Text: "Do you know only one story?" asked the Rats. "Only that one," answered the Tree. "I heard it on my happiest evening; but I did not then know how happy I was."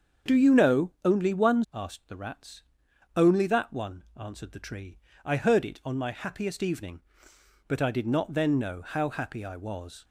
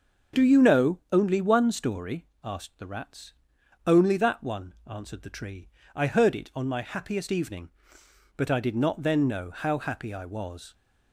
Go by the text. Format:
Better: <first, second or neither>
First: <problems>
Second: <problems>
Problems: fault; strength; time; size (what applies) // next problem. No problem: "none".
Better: second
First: starts louder than the rest; strong; until 1.4 s; 7 dB // skips "story"; at 1.6 s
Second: starts louder than the rest; until 1.4 s; 6.5 dB